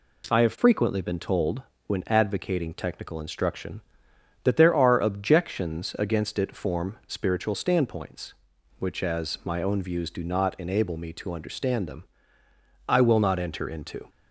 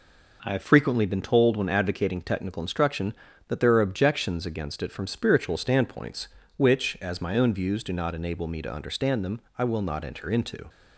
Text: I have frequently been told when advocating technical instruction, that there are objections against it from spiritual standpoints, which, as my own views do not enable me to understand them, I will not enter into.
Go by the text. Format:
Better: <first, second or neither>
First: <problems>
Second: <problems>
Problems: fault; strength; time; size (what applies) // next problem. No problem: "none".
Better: second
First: pauses between "told" and "when"; slight; at 1.6 s; 0.24 s long // says "form" for "from"; at 6.5 s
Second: none